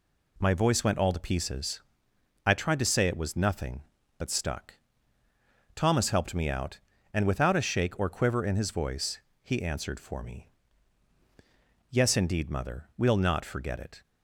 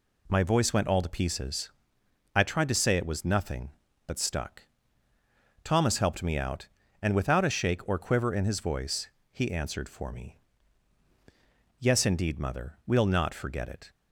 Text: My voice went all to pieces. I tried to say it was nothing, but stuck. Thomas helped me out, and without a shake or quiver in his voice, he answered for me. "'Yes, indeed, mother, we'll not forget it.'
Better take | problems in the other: neither | none

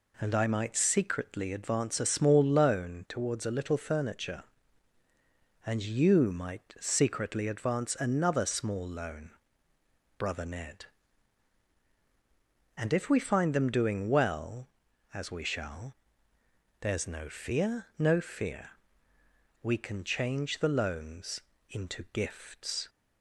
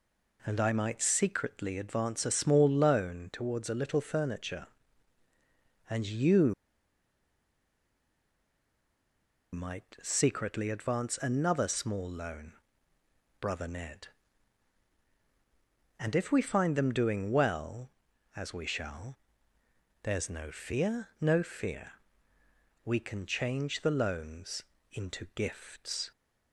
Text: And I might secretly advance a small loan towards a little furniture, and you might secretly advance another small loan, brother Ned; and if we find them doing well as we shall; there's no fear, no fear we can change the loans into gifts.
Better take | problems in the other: first | pauses between "you" and "might"; strong; at 6.5 s; 2.9 s long // pauses between "fear" and "we"; noticeable; at 21.9 s; 0.90 s long; noticeable in the first // pauses between "loans" and "into"; slight; at 24.6 s; 0.28 s long; slight in the first

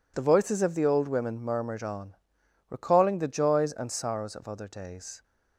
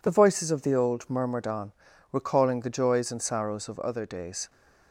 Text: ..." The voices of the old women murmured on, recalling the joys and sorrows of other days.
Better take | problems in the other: first | skips "women"; at 1.0 s

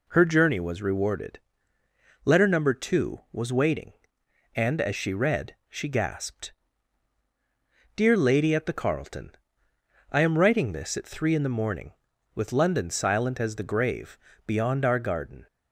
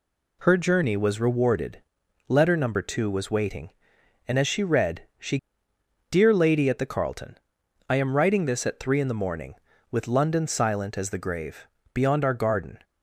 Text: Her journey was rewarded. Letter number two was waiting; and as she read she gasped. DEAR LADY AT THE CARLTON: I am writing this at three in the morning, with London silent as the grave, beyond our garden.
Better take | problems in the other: first | pauses between "read" and "she"; slight; at 5.0 s; 0.16 s long // skips "gasped"; at 5.7 s

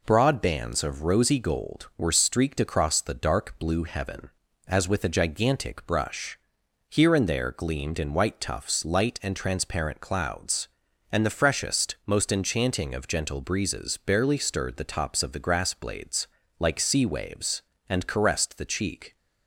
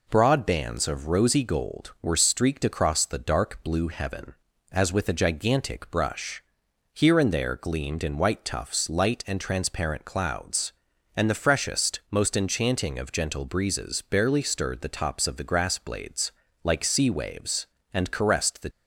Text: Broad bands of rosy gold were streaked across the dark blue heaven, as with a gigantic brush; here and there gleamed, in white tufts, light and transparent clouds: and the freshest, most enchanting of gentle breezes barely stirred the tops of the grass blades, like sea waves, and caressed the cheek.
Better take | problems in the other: first | stops before "cheek"; at 18.7 s

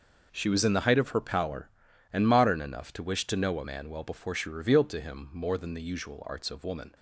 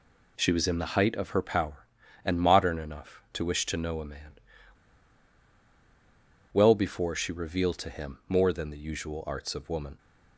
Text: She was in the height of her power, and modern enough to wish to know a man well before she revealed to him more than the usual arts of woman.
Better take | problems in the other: first | pauses between "man" and "well"; strong; at 4.3 s; 2.1 s long

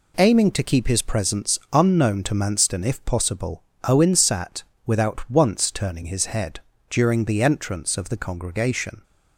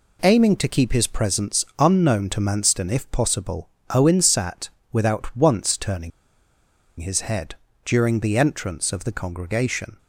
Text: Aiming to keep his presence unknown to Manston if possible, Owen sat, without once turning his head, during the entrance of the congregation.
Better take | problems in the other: first | pauses between "turning" and "his"; noticeable; at 6.1 s; 0.89 s long

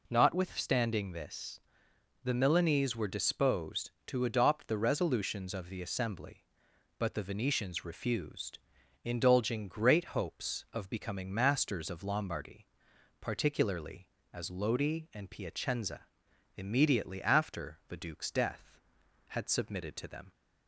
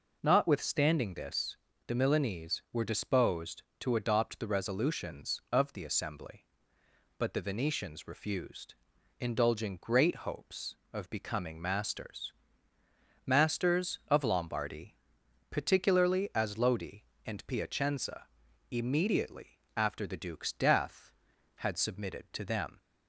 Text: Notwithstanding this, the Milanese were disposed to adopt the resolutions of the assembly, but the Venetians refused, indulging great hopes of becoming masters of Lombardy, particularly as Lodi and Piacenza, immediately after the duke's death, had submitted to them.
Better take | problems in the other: first | says "masters" twice; at 13.2 s // pauses between "immediately" and "after"; slight; at 19.5 s; 0.16 s long

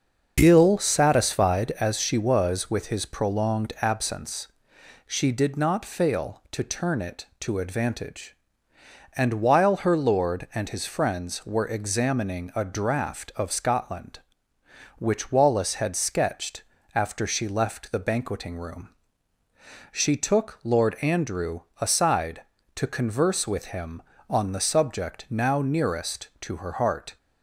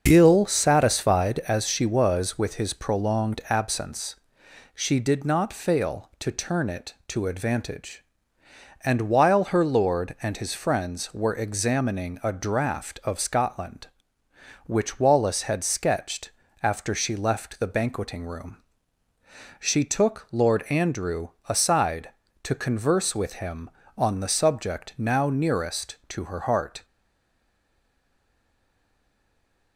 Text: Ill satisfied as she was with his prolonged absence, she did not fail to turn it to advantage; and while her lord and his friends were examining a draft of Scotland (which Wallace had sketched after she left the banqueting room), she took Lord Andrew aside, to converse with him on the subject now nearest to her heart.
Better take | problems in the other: first | starts louder than the rest; until 1.0 s; 6.5 dB; also in the first // pauses between "sketched" and "after"; slight; at 16.3 s; 0.32 s long; slight in the first // pauses between "Andrew" and "aside"; slight; at 21.3 s; 0.18 s long; slight in the first // stays silent after the last word; strong; from 26.8 s on; 2.9 s long

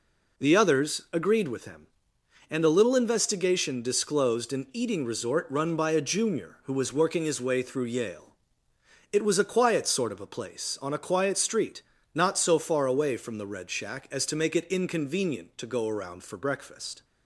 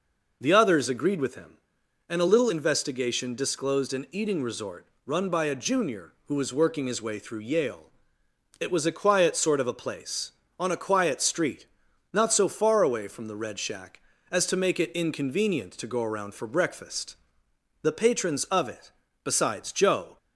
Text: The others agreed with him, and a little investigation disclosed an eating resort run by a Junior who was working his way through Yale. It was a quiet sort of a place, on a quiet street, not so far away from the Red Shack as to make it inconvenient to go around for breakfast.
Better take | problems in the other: first | pauses between "resort" and "run"; slight; at 4.8 s; 0.18 s long // goes on to say "The patrons of it besides Joe"; strong; from 17.8 s on; 2.3 s long

